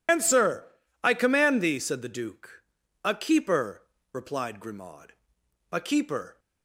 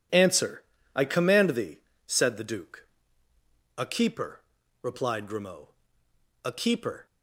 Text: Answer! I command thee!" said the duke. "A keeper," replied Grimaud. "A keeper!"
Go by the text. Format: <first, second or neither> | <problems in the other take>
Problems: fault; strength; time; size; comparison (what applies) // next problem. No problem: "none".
second | loses the start of "Answer"; at 0.0 s; 130 ms